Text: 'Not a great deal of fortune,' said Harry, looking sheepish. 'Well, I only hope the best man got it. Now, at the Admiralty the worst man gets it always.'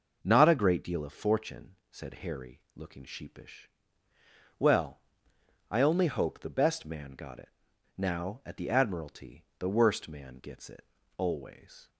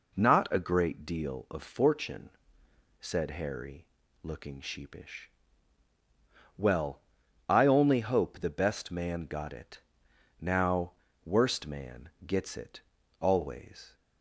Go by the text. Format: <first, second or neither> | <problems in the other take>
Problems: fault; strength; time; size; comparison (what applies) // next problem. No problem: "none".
first | skips "at the Admiralty the"; at 11.0 s // pauses between "man" and "gets"; slight; at 12.1 s; 0.16 s long // pauses between "it" and "always"; at 12.8 s; 0.40 s long; slight in the first